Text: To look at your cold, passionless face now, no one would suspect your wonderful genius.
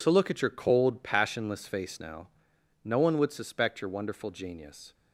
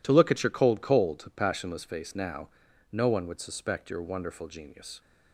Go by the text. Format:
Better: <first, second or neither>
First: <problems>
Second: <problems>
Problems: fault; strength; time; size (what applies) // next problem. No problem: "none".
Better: first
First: none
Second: says "cold" twice; at 0.8 s